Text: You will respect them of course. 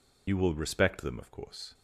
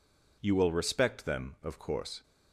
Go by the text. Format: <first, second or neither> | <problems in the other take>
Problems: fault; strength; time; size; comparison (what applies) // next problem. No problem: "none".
second | loses the start of "You"; at 0.2 s; 40 ms